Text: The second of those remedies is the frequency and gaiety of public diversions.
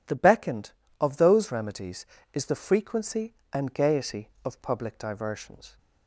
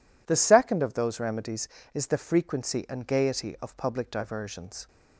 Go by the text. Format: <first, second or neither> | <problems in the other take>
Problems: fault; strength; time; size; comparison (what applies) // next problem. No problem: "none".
second | says "beckoned" for "second"; at 0.1 s